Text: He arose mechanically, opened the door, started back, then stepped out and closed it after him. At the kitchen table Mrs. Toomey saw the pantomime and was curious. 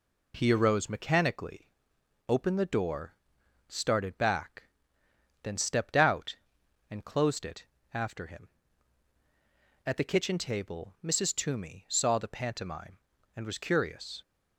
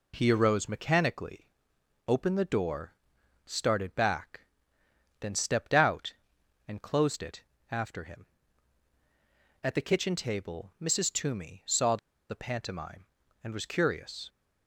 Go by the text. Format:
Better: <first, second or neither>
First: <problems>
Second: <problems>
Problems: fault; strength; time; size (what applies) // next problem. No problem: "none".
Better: first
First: pauses between "it" and "after"; slight; at 7.6 s; 0.26 s long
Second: pauses between "it" and "after"; slight; at 7.4 s; 0.26 s long // pauses between "saw" and "the"; slight; at 11.9 s; 0.33 s long